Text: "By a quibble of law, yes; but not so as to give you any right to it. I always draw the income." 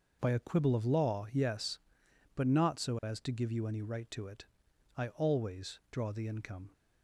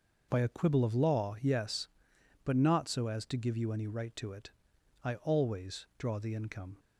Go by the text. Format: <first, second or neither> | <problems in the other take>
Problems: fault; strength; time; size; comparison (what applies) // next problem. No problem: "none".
neither | none